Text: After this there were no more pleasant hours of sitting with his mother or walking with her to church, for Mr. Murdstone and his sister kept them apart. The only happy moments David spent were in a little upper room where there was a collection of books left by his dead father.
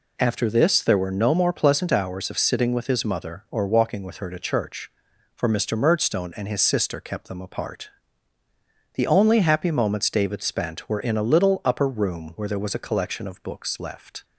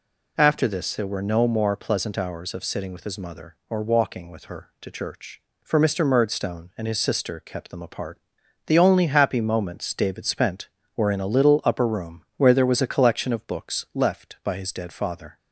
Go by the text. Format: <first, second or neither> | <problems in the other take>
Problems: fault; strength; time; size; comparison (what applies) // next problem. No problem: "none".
second | stops before "by his dead father"; at 14.2 s